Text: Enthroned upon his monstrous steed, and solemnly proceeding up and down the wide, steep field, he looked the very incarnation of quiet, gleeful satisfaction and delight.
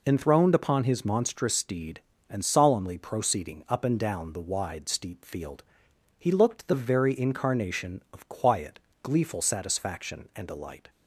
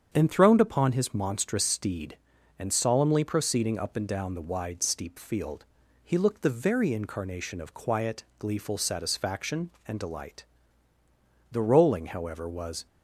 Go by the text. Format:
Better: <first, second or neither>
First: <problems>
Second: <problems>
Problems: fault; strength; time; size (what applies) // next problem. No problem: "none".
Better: first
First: none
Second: starts louder than the rest; strong; until 1.1 s; 8 dB // goes on to say "The rolling however was"; from 11.5 s on; 1.3 s long